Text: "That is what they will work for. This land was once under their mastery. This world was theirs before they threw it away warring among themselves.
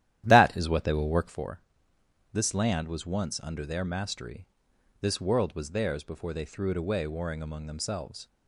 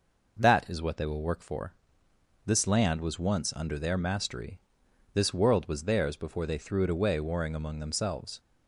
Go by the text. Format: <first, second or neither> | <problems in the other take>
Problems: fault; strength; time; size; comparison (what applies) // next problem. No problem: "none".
second | starts louder than the rest; strong; until 1.6 s; 12 dB